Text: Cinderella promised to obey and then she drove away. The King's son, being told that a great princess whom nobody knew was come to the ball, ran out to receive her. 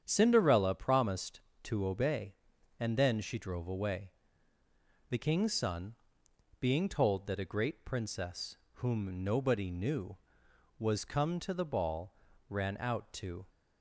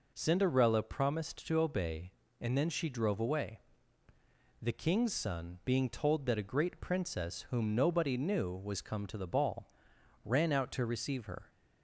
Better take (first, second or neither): second